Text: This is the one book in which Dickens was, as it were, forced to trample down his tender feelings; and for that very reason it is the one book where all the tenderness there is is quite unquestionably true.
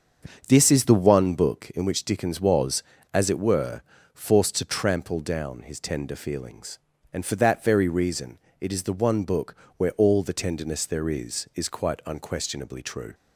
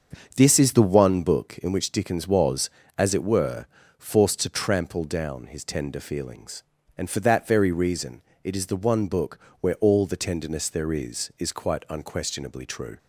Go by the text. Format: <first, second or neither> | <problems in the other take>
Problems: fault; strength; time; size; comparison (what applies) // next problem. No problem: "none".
neither | starts louder than the rest; the same in both // pauses between "reason" and "it"; slight; the same in both // pauses between "book" and "where"; slight; the same in both